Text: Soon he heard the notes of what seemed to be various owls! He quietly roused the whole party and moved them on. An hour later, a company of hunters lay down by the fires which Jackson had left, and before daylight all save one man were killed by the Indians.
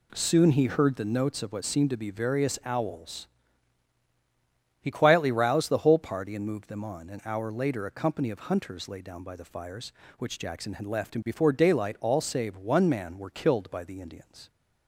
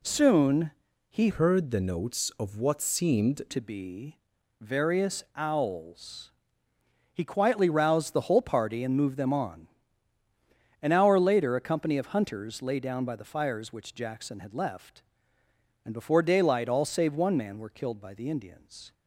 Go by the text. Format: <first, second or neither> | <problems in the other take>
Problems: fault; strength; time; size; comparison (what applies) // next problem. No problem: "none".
first | pauses between "Soon" and "he"; at 0.7 s; 0.38 s long // changes voice from "heard" to "seemed"; from 1.2 to 3.4 s; 2.2 s long // pauses between "be" and "various"; at 4.1 s; 0.42 s long